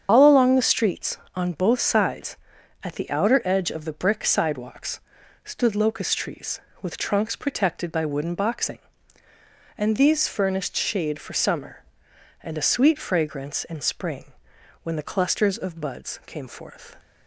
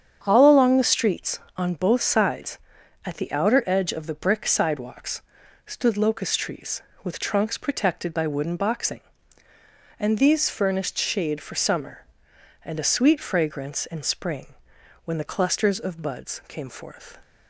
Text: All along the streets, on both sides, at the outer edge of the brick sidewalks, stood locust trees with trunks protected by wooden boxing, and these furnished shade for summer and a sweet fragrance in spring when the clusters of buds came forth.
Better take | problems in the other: second | loses the start of "All"; at 0.0 s; 100 ms // starts louder than the rest; strong; until 1.1 s; 8 dB; strong in the second // pauses between "spring" and "when"; noticeable; at 14.3 s; 0.52 s long; noticeable in the second

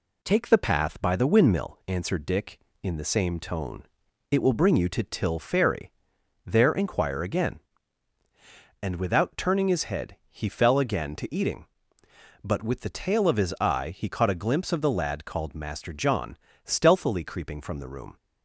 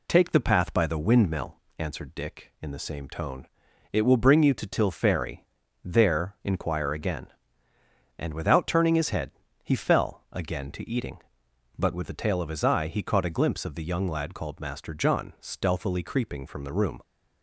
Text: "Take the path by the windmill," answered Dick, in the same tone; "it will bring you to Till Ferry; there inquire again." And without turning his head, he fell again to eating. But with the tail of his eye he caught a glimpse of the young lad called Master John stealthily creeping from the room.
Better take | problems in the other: second | skips "young"; at 14.9 s // pauses between "John" and "stealthily"; slight; at 16.3 s; 0.26 s long

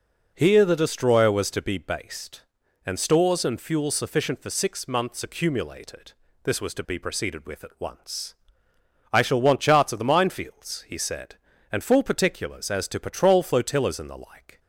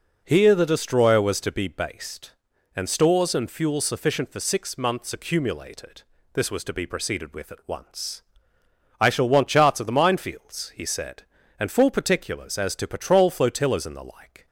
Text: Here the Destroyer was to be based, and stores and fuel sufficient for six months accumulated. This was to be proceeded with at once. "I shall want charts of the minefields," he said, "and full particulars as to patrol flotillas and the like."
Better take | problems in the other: neither | none

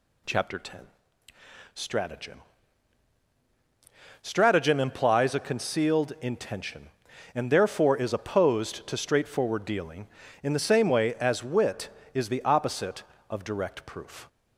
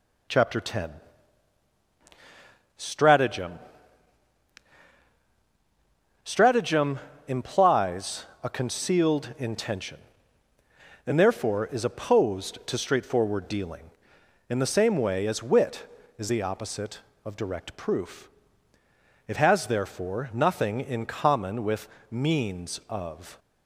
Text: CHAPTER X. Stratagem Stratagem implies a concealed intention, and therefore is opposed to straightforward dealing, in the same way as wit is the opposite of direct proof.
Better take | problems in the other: first | pauses between "Stratagem" and "Stratagem"; strong; at 3.5 s; 2.6 s long; strong in the first // pauses between "Stratagem" and "implies"; slight; at 6.9 s; 0.26 s long // pauses between "implies" and "a"; slight; at 8.2 s; 0.18 s long // goes on to say "It has therefore nothing in common with means of"; strong; from 19.2 s on; 4.1 s long

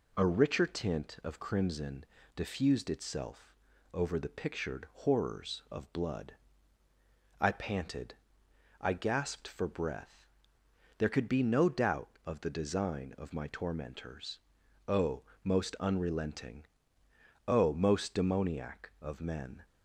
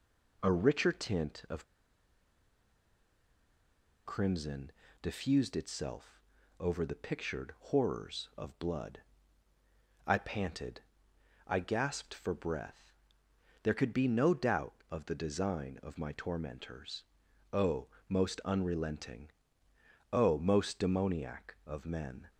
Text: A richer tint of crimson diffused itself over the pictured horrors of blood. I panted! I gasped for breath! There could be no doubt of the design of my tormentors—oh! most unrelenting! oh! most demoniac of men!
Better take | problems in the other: first | pauses between "of" and "crimson"; strong; at 1.6 s; 2.4 s long // pauses between "crimson" and "diffused"; slight; at 4.7 s; 0.30 s long; slight in the first // pauses between "itself" and "over"; slight; at 6.2 s; 0.36 s long; slight in the first

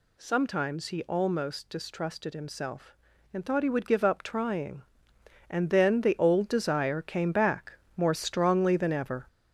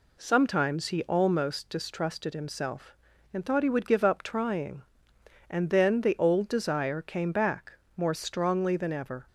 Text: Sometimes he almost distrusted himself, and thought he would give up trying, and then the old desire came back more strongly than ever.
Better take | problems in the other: second | gets louder; noticeable; throughout; 5.5 dB // pauses between "back" and "more"; slight; at 7.7 s; 0.20 s long; slight in the second

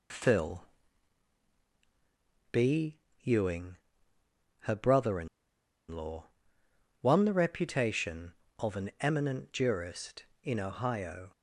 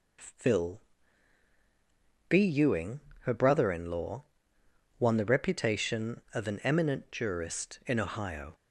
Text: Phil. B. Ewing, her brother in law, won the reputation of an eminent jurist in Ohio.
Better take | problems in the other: second | pauses between "in" and "law"; noticeable; at 5.2 s; 0.63 s long

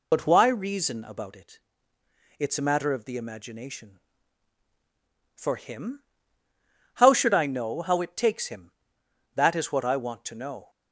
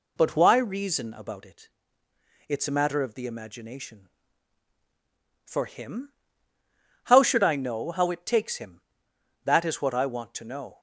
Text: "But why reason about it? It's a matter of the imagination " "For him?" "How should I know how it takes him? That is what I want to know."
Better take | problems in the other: second | loses the start of "But"; at 0.1 s; 40 ms

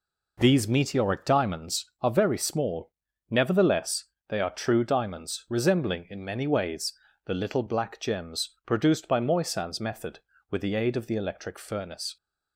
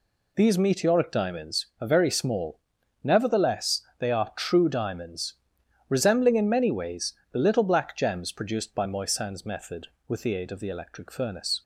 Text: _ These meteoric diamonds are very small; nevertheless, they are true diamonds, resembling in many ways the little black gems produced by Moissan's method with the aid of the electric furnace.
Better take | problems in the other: neither | pauses between "ways" and "the"; slight; the same in both

